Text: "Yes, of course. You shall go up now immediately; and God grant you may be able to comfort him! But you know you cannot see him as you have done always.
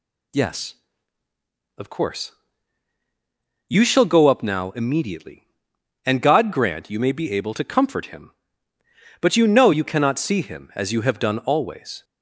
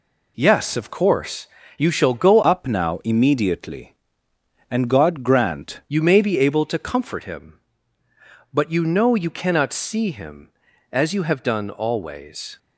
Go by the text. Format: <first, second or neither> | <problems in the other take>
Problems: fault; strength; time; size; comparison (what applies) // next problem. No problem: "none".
first | changes voice from "up" to "grant"; from 2.4 to 5.8 s; 3.4 s long